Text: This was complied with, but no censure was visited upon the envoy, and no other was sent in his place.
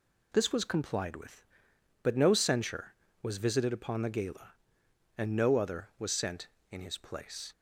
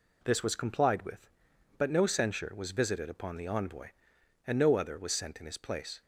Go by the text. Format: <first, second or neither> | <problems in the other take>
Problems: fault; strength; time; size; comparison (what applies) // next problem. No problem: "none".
second | says "gala" for "envoy"; at 4.0 s